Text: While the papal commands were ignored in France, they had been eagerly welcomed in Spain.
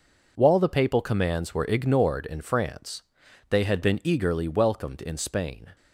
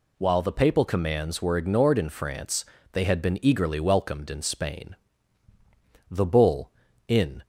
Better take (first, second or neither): first